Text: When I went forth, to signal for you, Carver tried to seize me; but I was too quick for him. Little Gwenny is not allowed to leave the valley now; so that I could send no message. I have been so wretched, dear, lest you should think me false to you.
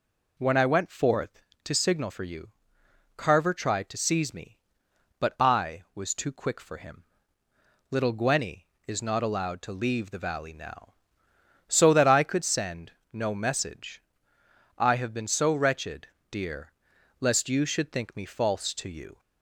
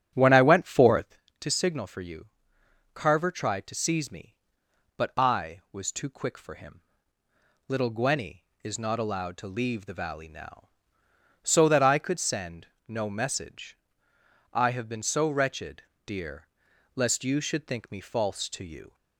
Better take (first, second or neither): first